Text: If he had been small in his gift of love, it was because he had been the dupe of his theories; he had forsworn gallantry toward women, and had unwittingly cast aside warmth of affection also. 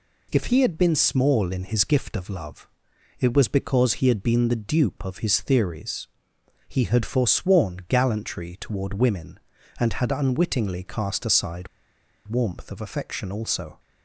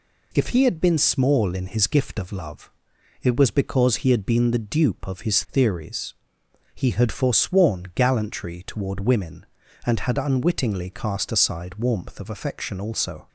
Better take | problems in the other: second | pauses between "aside" and "warmth"; noticeable; at 11.6 s; 0.59 s long

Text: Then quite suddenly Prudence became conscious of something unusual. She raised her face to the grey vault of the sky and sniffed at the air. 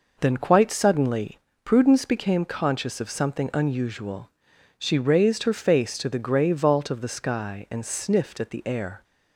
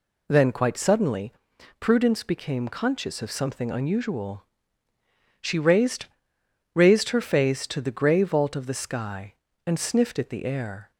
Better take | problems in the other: first | pauses between "suddenly" and "Prudence"; noticeable; at 1.3 s; 0.46 s long; slight in the first // says "raised" twice; at 6.7 s

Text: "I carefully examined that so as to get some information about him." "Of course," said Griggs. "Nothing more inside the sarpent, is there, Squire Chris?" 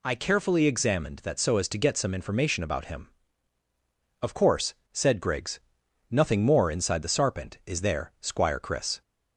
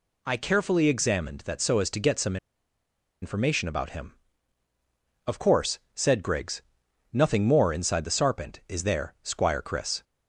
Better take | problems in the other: first | pauses between "some" and "information"; noticeable; at 2.3 s; 0.85 s long

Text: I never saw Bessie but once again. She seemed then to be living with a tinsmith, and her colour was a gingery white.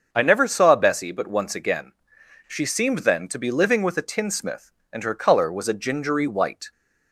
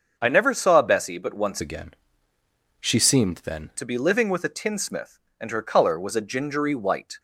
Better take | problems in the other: first | starts louder than the rest; until 1.1 s; 6.5 dB; also in the first // changes voice from "again" to "then"; from 1.5 to 3.6 s; 2.1 s long

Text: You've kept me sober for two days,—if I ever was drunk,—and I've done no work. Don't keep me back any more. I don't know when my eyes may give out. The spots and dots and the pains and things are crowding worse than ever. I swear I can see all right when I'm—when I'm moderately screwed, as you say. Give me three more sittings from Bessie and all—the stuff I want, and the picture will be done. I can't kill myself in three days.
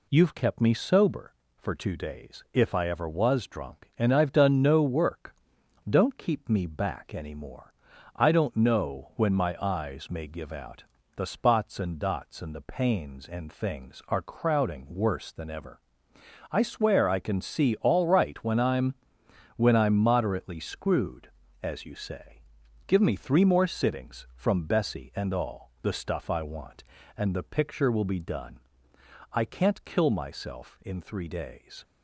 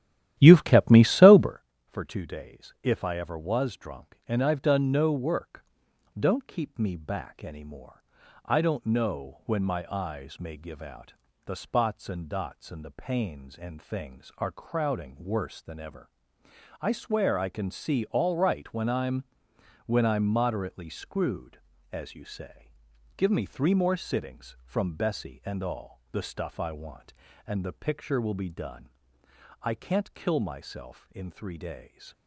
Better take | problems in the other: first | starts louder than the rest; strong; until 1.6 s; 12.5 dB

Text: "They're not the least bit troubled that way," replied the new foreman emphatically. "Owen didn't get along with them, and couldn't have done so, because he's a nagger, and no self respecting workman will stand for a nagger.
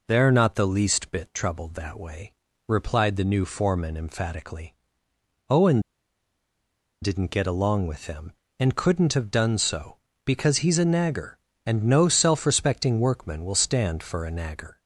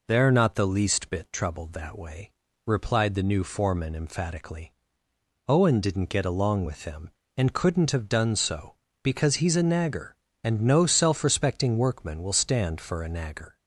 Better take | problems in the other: second | pauses between "Owen" and "didn't"; at 5.7 s; 1.2 s long

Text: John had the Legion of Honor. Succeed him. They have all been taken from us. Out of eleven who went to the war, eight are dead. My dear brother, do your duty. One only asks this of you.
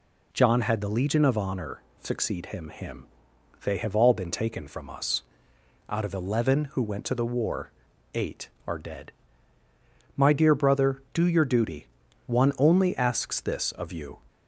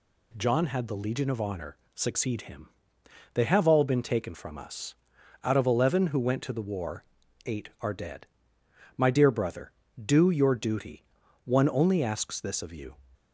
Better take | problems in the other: second | says "him" twice; at 2.6 s

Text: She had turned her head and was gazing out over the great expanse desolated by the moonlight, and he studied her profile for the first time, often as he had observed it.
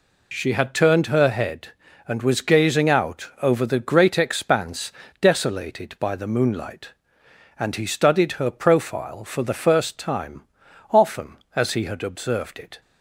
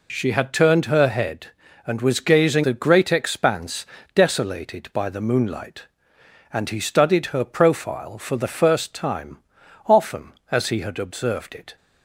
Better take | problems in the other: first | skips "out over"; at 2.6 s // pauses between "expanse" and "desolated"; slight; at 3.8 s; 0.30 s long; slight in the first

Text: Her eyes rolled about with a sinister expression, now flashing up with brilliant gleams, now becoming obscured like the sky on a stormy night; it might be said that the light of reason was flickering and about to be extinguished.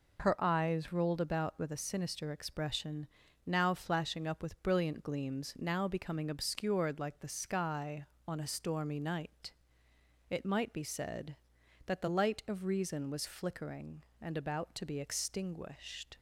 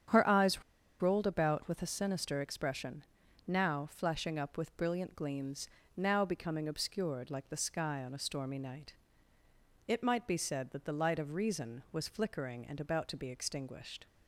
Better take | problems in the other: first | starts louder than the rest; strong; until 1.4 s; 8.5 dB // pauses between "eyes" and "rolled"; at 0.6 s; 0.39 s long

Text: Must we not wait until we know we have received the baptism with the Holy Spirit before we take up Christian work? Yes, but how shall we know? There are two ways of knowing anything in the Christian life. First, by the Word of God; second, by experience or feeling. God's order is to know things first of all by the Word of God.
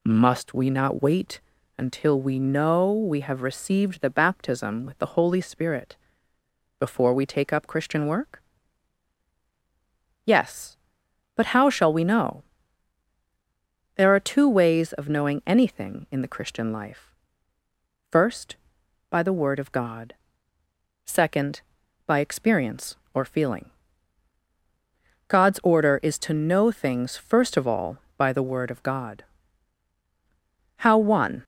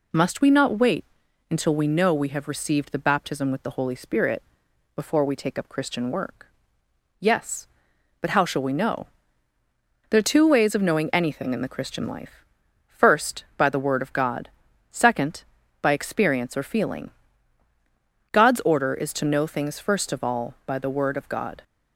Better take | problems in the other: second | pauses between "wait" and "until"; at 1.3 s; 0.38 s long; noticeable in the second // pauses between "Spirit" and "before"; noticeable; at 5.9 s; 0.80 s long; noticeable in the second // goes on to say "How one"; noticeable; from 30.7 s on; 0.66 s long

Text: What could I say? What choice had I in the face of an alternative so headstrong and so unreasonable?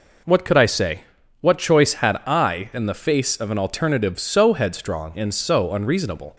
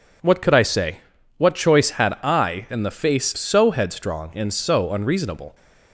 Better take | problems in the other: first | skips "of an alternative"; at 3.3 s

